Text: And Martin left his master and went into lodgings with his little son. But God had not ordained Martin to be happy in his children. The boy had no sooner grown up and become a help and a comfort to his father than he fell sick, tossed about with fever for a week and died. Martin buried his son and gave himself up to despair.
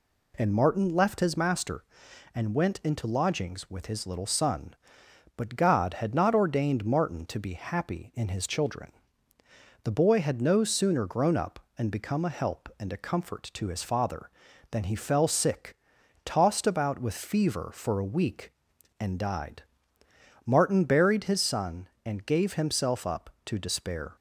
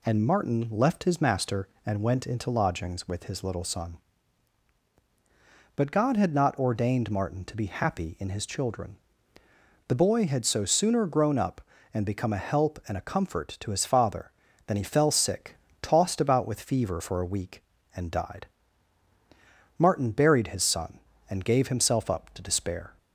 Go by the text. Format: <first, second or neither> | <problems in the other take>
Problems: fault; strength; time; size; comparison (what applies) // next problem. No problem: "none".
first | says "so" for "no"; at 10.4 s